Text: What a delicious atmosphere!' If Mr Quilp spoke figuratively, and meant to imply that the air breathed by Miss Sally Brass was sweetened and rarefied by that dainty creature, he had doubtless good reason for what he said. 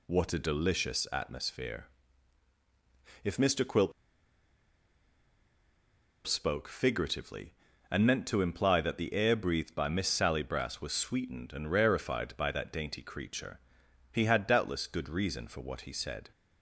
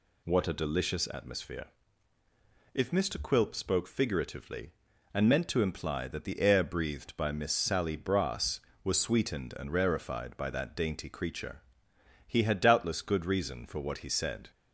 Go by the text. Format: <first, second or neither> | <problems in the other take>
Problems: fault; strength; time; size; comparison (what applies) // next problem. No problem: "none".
second | pauses between "Quilp" and "spoke"; strong; at 3.9 s; 2.3 s long